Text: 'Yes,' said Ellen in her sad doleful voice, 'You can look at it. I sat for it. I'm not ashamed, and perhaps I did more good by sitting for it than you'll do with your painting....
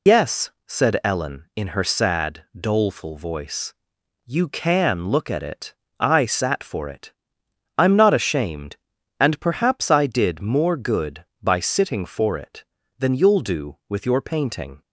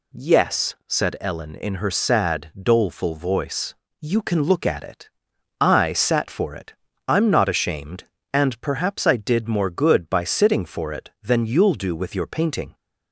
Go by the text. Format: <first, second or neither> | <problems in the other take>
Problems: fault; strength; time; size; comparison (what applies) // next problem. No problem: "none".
second | loses the start of "Yes"; at 0.0 s; 125 ms